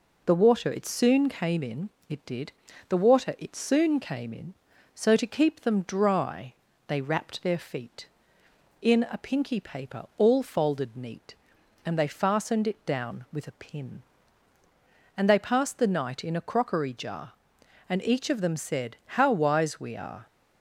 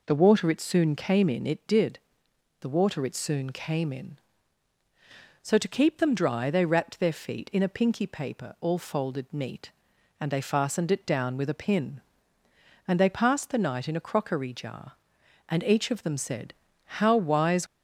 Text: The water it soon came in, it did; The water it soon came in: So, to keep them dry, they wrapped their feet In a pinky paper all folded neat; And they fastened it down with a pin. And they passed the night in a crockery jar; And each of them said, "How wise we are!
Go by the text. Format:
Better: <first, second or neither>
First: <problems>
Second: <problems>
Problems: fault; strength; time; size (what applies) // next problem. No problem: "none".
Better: first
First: none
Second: stops before "we are"; at 17.6 s